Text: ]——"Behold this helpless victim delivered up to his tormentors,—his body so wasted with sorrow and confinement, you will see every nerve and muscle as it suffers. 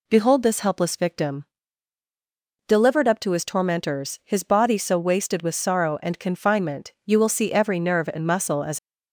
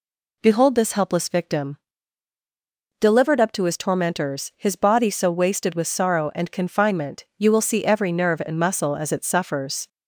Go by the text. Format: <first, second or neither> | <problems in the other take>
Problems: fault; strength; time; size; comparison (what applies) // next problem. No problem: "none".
second | pauses between "victim" and "delivered"; at 1.4 s; 1.2 s long; also in the second // stops before "it suffers"; at 8.7 s